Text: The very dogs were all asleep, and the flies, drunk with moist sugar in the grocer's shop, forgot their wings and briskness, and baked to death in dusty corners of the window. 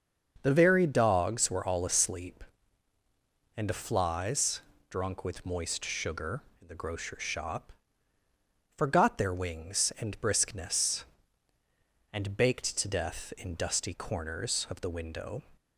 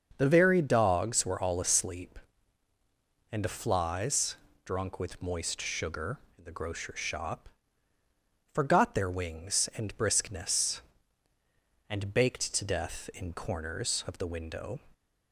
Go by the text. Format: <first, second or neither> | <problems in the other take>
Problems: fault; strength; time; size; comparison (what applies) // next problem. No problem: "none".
first | starts louder than the rest; until 1.1 s; 6.5 dB; also in the first // skips "dusty"; at 13.3 s